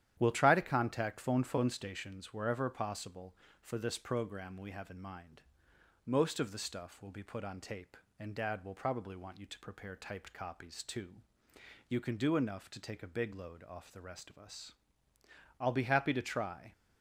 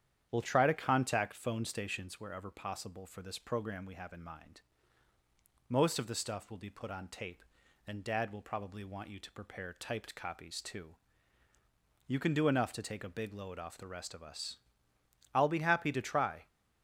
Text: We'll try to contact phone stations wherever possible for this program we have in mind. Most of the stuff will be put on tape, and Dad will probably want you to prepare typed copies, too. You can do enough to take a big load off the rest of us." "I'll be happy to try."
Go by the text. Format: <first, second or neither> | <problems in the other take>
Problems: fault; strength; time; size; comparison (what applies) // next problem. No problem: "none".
second | starts louder than the rest; strong; until 1.2 s; 11 dB; strong in the second // says "phone" twice; at 1.4 s